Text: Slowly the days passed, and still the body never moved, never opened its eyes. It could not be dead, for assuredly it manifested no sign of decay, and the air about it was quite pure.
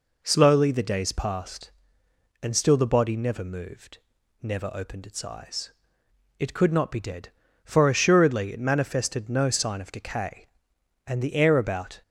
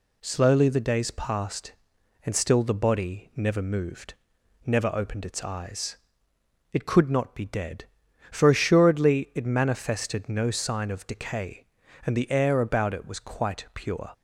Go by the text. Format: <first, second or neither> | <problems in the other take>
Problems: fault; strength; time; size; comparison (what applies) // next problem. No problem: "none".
second | stops before "it was quite pure"; at 12.0 s